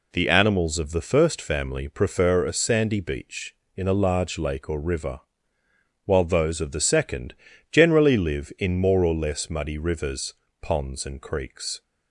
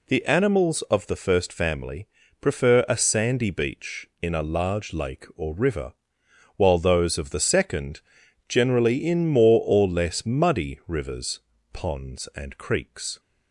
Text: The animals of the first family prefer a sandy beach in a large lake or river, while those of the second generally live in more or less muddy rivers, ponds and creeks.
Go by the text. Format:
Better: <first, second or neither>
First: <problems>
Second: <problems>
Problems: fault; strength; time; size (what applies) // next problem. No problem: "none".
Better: first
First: pauses between "second" and "generally"; slight; at 7.3 s; 0.36 s long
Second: pauses between "family" and "prefer"; slight; at 2.0 s; 0.34 s long // pauses between "second" and "generally"; noticeable; at 8.0 s; 0.46 s long // skips "live"; at 9.0 s